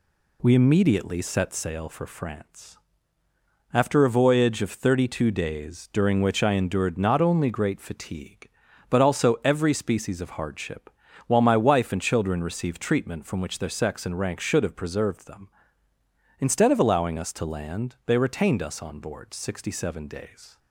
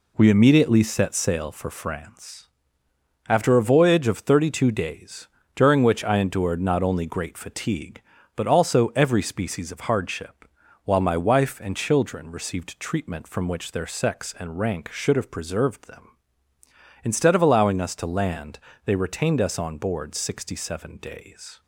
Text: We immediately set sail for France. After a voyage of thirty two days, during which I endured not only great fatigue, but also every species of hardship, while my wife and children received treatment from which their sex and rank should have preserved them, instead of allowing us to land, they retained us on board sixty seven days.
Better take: neither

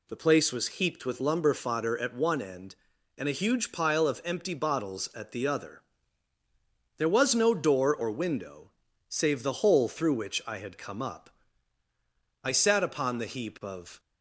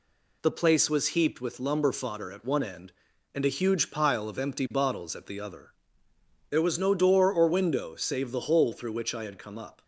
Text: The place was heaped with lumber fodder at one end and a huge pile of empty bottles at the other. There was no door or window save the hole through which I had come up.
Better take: second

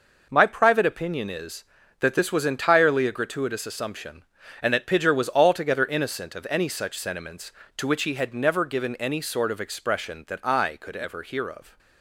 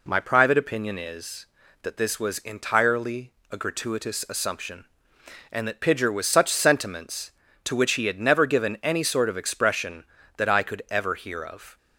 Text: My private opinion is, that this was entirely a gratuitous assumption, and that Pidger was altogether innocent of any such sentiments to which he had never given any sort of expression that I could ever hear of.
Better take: first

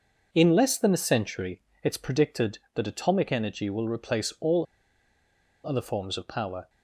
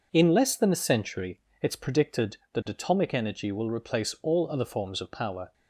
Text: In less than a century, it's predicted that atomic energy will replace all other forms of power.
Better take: second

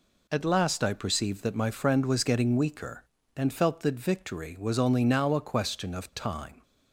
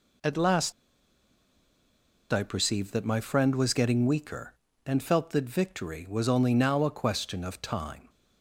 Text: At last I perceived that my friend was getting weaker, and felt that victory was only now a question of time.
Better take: first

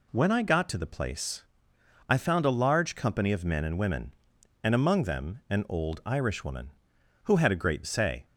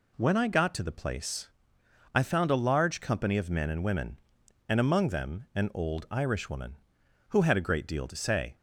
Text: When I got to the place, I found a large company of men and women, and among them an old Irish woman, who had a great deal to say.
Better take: second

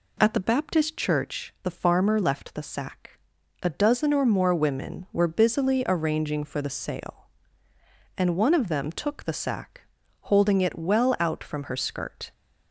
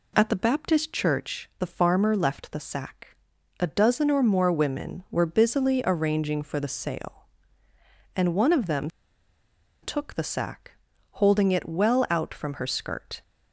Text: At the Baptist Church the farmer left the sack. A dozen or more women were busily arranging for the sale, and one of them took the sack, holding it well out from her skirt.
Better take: first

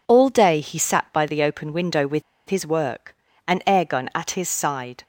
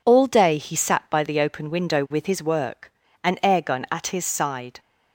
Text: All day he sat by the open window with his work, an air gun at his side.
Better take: second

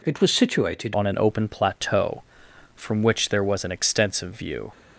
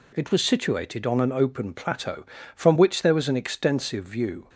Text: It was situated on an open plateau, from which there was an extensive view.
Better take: second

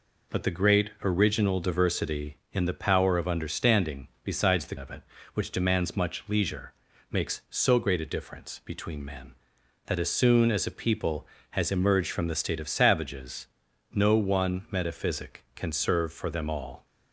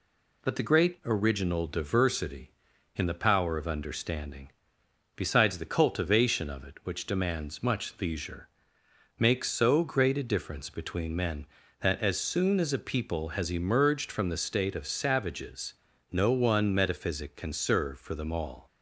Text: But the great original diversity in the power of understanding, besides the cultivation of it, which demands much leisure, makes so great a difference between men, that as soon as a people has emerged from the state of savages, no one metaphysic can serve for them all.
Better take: second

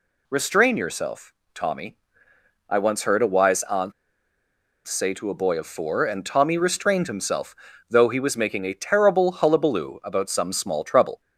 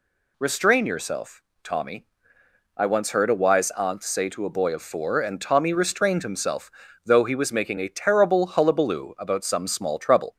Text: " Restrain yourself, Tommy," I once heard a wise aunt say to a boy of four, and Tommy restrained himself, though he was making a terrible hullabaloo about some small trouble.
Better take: second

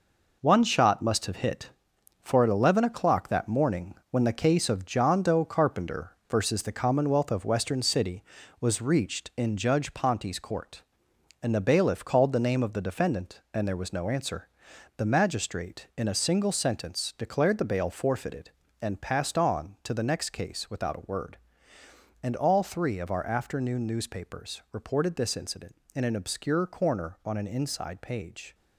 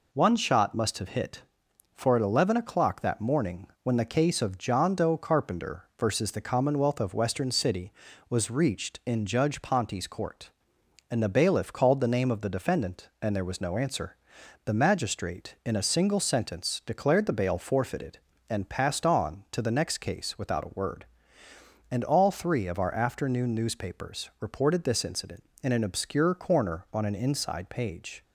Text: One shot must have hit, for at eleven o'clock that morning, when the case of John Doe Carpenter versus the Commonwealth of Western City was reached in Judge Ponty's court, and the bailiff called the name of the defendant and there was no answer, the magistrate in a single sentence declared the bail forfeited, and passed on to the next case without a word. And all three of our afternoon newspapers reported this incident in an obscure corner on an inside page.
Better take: second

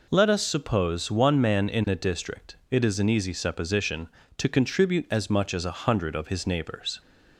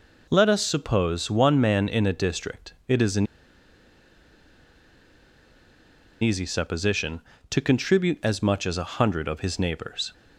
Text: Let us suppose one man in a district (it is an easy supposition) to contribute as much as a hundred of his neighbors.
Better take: first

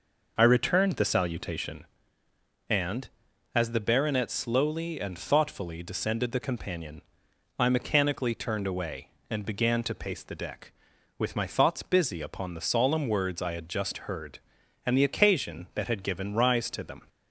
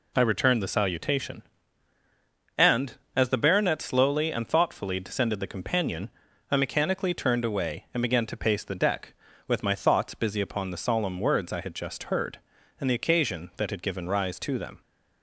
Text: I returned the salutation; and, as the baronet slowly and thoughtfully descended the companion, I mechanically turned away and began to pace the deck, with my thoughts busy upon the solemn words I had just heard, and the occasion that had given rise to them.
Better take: second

